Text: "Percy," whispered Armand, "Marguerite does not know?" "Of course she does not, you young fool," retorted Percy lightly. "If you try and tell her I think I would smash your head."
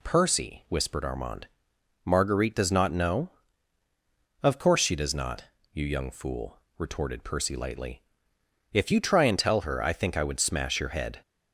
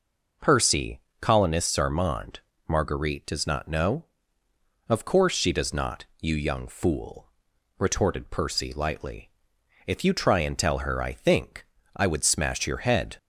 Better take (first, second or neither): first